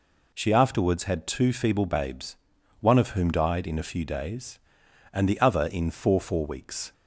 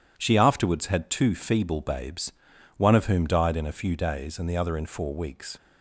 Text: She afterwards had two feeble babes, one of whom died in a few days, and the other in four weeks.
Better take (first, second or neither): second